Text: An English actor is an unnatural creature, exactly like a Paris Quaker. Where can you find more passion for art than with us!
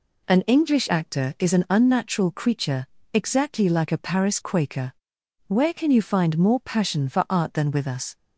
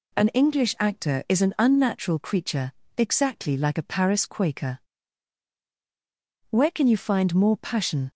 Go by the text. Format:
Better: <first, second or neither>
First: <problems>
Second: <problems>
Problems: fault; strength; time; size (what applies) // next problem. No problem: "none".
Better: first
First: none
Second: stops before "for art than with us"; at 8.1 s